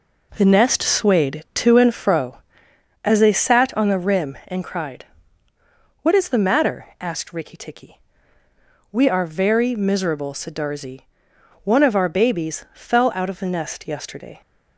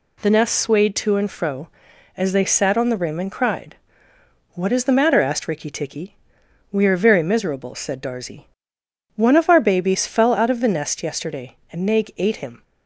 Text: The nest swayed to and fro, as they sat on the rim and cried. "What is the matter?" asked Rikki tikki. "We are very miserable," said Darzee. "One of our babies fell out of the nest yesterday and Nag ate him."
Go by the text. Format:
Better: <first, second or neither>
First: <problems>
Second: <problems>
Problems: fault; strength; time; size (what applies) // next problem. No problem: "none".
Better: second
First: stops before "and Nag ate him"; at 14.4 s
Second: none